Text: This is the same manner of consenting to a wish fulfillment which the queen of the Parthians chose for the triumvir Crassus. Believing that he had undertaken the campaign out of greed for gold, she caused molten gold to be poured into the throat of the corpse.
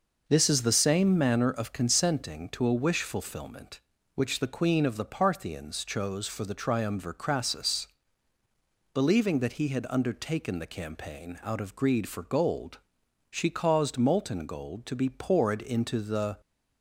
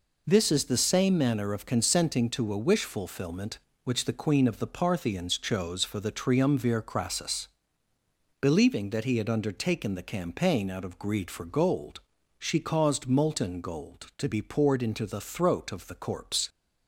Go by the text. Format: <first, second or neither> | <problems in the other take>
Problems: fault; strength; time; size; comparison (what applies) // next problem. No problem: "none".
second | stops before "throat of the corpse"; at 16.4 s